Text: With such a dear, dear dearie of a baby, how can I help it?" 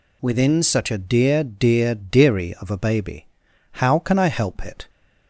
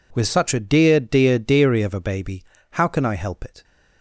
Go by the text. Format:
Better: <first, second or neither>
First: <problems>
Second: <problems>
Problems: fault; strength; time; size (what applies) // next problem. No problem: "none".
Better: second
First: says "Within" for "With"; at 0.2 s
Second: none